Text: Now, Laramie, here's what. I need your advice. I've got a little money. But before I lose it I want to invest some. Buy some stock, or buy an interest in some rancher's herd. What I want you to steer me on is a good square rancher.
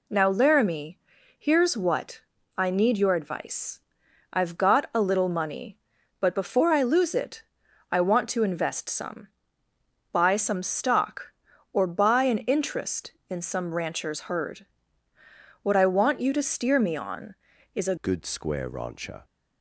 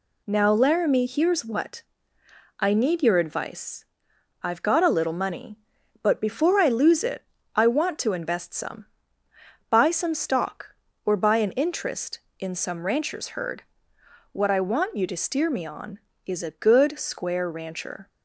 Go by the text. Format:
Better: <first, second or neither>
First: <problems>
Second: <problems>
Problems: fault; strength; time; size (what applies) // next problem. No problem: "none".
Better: second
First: pauses between "it" and "I"; noticeable; at 7.4 s; 0.50 s long // changes voice at "good"; from 17.9 s on; 1.3 s long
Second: pauses between "it" and "I"; slight; at 7.2 s; 0.32 s long